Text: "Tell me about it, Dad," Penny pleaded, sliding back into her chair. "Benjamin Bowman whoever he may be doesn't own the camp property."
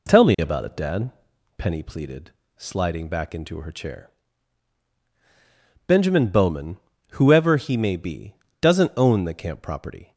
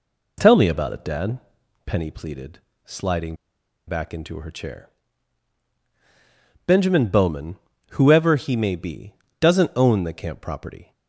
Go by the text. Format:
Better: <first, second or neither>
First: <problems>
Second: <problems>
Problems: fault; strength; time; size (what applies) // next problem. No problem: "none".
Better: first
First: pauses between "Bowman" and "whoever"; slight; at 6.7 s; 0.34 s long // pauses between "be" and "doesn't"; slight; at 8.3 s; 0.24 s long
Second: pauses between "sliding" and "back"; noticeable; at 3.3 s; 0.52 s long // pauses between "Bowman" and "whoever"; slight; at 7.5 s; 0.34 s long // pauses between "be" and "doesn't"; slight; at 9.1 s; 0.24 s long